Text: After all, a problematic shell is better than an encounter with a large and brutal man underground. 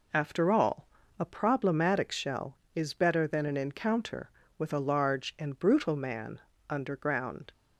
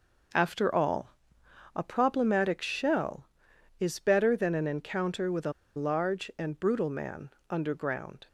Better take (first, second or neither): first